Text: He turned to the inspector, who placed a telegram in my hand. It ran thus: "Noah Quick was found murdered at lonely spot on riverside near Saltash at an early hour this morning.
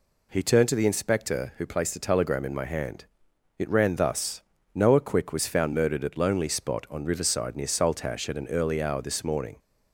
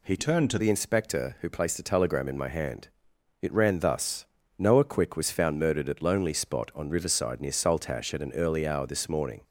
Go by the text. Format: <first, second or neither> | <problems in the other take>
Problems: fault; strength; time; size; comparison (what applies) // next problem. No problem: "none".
first | changes voice from "turned" to "to"; from 0.1 to 0.5 s; 0.4 s long